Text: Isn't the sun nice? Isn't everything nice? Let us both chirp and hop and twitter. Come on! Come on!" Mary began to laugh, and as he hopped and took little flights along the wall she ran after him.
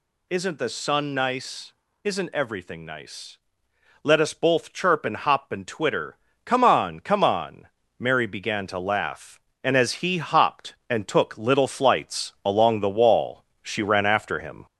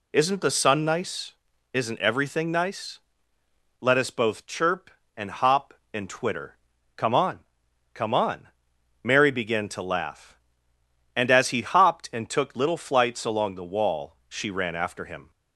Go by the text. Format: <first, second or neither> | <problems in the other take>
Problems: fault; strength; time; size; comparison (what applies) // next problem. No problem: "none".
second | gets louder; slight; throughout; 3 dB // pauses between "wall" and "she"; slight; at 13.4 s; 0.20 s long